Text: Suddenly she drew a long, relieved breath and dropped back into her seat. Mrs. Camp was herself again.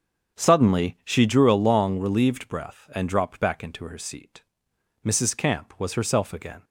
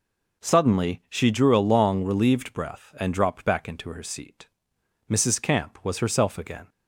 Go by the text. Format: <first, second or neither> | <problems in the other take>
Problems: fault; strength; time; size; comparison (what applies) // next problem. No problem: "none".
second | starts louder than the rest; until 1.7 s; 7 dB